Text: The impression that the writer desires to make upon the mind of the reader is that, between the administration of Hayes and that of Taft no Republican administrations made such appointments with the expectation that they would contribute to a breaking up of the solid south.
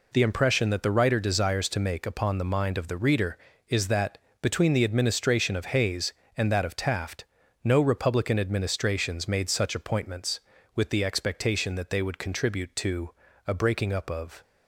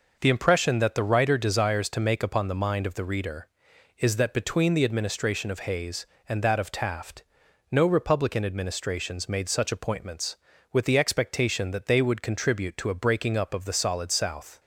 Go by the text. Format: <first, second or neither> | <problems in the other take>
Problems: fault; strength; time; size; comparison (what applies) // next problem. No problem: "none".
second | pauses between "Taft" and "no"; at 7.2 s; 0.40 s long; noticeable in the second // pauses between "to" and "a"; slight; at 13.1 s; 0.36 s long // stops before "the solid south"; at 14.4 s